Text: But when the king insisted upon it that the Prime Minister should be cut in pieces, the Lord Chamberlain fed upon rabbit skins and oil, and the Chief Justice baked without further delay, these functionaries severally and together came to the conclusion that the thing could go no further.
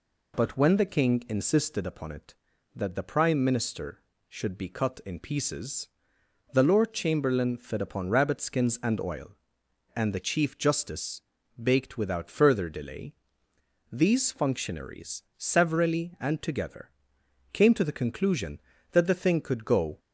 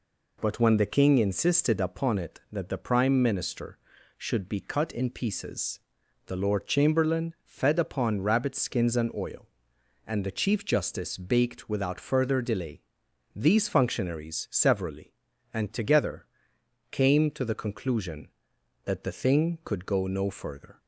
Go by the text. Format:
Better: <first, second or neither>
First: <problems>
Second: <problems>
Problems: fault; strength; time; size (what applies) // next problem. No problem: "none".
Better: second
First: pauses between "Justice" and "baked"; at 11.2 s; 0.40 s long // pauses between "together" and "came"; noticeable; at 16.9 s; 0.62 s long // stops before "no further"; at 19.9 s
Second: pauses between "together" and "came"; noticeable; at 16.2 s; 0.66 s long